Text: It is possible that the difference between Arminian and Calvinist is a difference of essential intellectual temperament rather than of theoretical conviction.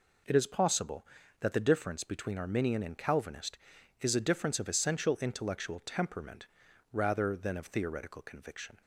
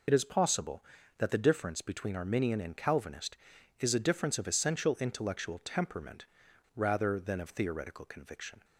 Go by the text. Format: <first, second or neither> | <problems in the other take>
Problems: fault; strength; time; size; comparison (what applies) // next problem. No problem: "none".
first | loses the start of "It"; at 0.0 s; 40 ms // pauses between "temperament" and "rather"; noticeable; at 6.2 s; 0.50 s long; noticeable in the first